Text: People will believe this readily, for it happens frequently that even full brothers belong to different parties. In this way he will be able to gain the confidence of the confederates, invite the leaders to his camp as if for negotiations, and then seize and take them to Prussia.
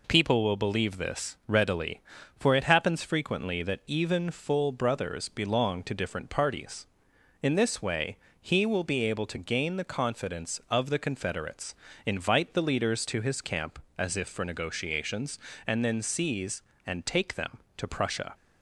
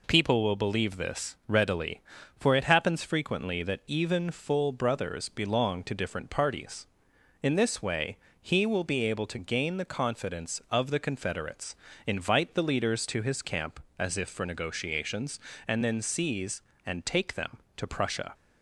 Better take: neither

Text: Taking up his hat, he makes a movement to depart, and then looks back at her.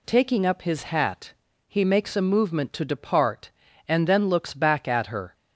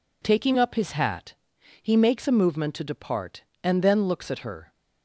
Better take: first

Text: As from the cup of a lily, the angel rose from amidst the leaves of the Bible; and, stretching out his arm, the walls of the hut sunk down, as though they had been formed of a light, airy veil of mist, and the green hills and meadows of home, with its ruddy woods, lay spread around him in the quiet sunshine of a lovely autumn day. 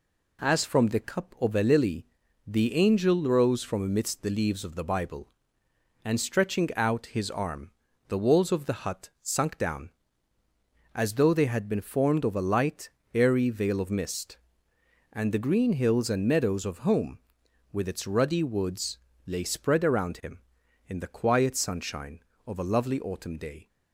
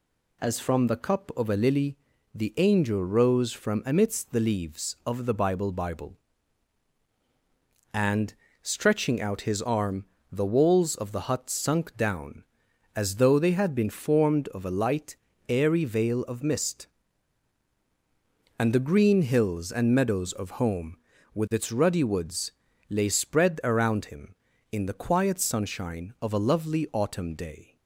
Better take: first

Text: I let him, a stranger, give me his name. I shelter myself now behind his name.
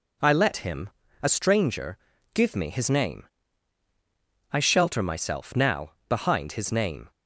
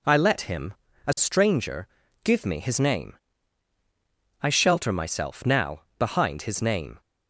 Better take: neither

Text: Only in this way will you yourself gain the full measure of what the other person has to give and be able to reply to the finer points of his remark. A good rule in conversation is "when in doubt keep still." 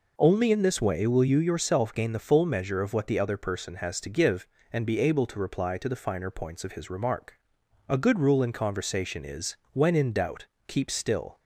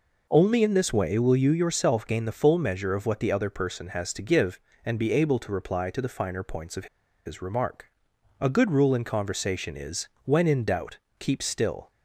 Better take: first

